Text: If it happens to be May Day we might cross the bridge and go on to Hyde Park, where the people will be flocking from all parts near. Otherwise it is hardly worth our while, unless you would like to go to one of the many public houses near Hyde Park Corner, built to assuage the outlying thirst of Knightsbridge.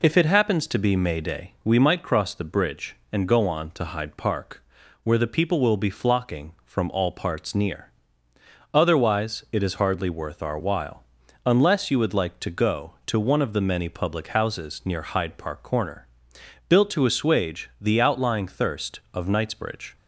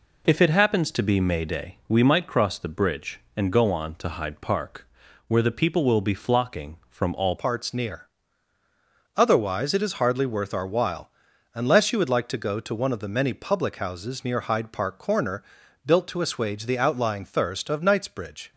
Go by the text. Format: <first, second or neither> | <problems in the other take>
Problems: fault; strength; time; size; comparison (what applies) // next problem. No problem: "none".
first | changes voice at "parts"; from 7.3 s on; 11.2 s long